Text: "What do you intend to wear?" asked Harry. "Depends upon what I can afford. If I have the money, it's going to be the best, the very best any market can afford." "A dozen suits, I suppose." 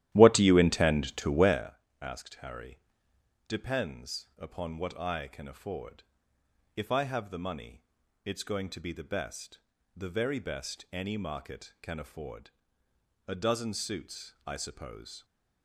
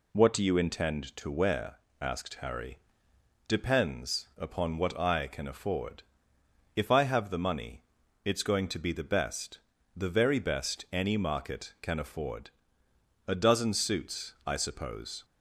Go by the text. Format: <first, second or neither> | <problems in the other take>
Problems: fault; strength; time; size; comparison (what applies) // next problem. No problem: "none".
second | starts louder than the rest; strong; until 1.7 s; 13 dB